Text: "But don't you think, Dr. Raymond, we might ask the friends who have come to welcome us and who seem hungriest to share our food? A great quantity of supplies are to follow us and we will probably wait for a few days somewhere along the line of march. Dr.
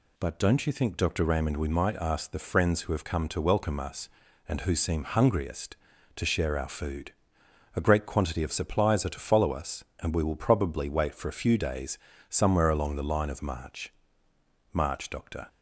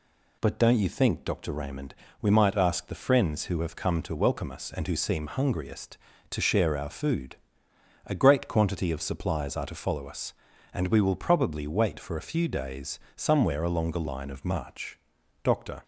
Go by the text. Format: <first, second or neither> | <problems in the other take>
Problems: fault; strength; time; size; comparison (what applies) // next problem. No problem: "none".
second | pauses between "days" and "somewhere"; slight; at 11.9 s; 0.32 s long; slight in the second // says "march" twice; at 14.7 s